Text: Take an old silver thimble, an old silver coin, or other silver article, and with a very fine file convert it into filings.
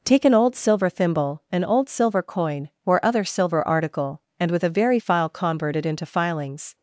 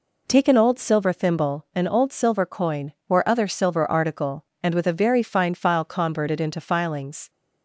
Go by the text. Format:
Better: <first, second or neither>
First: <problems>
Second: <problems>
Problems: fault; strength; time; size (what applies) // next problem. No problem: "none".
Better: second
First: skips "fine"; at 4.9 s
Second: none